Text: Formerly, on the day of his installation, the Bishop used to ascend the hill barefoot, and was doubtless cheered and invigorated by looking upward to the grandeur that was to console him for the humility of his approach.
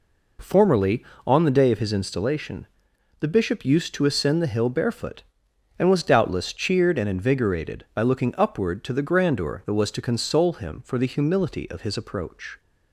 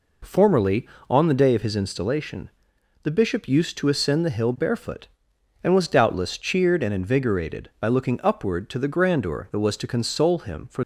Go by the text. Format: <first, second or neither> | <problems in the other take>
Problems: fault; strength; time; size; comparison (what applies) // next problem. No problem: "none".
first | stops before "the humility of his approach"; at 10.8 s